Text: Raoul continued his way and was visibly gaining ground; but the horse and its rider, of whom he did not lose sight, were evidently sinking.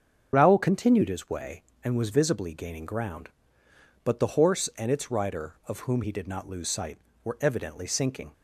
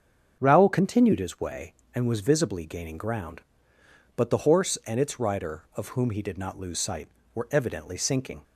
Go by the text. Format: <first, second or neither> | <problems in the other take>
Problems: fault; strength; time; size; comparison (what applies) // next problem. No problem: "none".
second | loses the start of "Raoul"; at 0.3 s; 35 ms // starts louder than the rest; until 1.3 s; 7 dB; also in the second